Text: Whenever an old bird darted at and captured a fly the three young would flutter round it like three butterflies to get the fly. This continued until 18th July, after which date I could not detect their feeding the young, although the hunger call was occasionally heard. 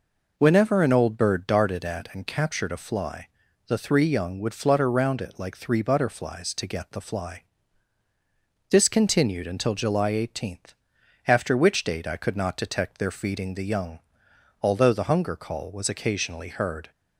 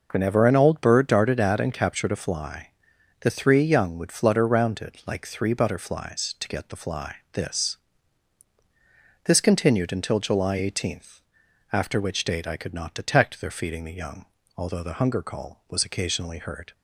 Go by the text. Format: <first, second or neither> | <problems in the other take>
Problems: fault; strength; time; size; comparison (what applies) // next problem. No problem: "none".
first | pauses between "fly" and "the"; noticeable; at 2.6 s; 0.54 s long; also in the first // says "This" twice; at 9.2 s